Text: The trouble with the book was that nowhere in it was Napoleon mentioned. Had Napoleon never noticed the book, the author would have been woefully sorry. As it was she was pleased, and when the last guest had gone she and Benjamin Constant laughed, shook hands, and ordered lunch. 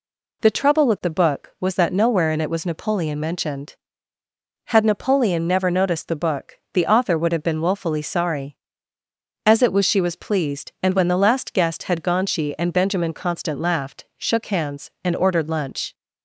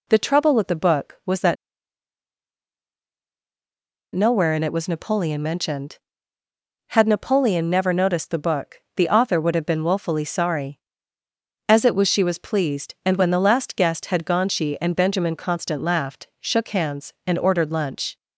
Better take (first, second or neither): first